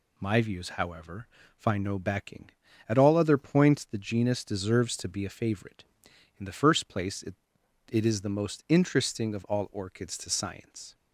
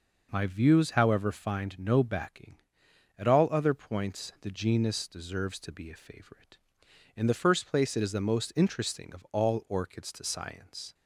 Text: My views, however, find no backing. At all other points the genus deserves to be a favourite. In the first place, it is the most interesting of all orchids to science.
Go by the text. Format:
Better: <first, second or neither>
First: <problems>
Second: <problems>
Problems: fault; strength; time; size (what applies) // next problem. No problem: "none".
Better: second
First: says "it" twice; at 7.8 s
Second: none